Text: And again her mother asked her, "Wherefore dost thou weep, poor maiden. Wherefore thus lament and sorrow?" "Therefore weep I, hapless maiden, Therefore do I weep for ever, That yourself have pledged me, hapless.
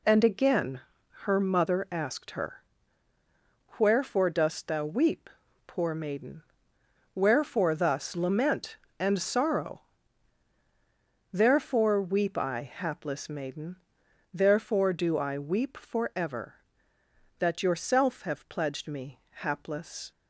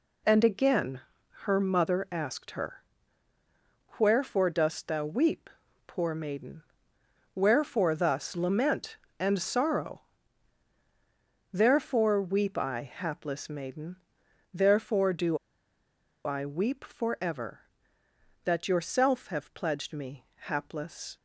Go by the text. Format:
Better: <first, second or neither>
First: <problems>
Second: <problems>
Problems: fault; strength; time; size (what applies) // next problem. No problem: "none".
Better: first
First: pauses between "again" and "her"; at 0.8 s; 0.42 s long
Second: pauses between "again" and "her"; at 1.0 s; 0.42 s long // pauses between "do" and "I"; noticeable; at 15.3 s; 0.89 s long